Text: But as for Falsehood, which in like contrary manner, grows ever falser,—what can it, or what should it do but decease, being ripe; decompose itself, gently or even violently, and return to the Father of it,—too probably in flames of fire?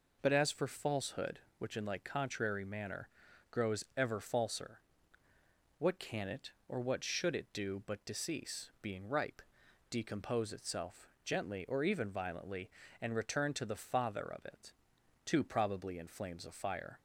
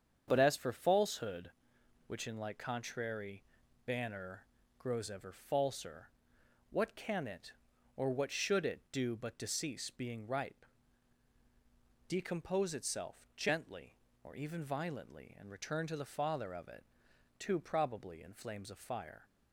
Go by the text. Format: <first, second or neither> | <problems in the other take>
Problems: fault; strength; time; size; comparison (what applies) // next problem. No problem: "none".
first | starts louder than the rest; strong; until 1.2 s; 7.5 dB // says "banner" for "manner"; at 3.8 s